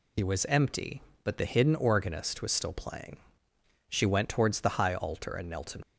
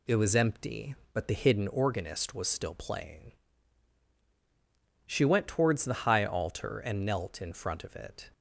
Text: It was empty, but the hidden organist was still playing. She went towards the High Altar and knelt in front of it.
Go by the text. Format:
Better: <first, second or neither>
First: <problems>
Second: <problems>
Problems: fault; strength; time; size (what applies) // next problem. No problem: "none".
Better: second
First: stops before "front of it"; at 5.8 s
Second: none